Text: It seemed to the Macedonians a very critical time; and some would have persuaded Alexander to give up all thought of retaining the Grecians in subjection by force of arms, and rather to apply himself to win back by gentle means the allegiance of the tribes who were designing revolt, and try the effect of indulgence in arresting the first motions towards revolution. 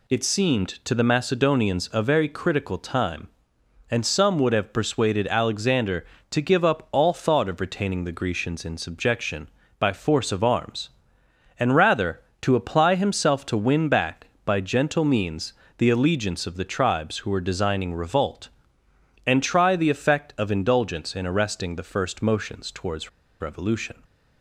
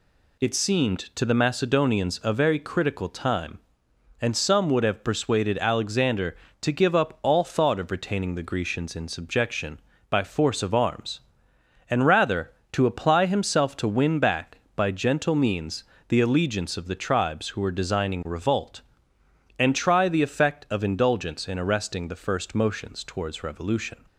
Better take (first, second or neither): second